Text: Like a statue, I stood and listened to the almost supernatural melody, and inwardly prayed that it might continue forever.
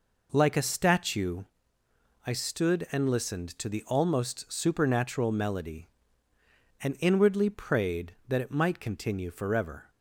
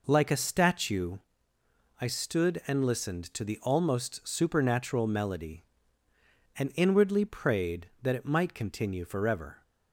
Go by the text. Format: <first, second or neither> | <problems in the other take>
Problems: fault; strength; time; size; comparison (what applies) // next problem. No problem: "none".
neither | none